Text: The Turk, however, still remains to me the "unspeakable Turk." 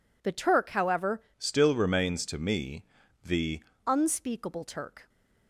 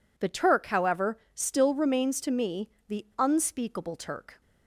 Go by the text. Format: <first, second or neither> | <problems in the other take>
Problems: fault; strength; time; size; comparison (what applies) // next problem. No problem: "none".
second | changes voice from "still" to "the"; from 1.3 to 3.6 s; 2.3 s long // pauses between "me" and "the"; at 2.8 s; 0.42 s long; slight in the second